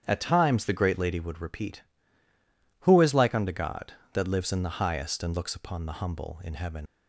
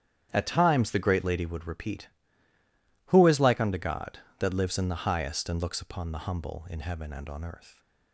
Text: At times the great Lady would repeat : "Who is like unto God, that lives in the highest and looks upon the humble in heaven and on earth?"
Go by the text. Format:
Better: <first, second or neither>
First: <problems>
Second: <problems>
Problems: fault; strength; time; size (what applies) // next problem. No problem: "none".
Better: second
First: starts louder than the rest; strong; until 1.0 s; 9 dB // stops before "and on earth"; at 6.8 s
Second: starts louder than the rest; strong; until 1.3 s; 10 dB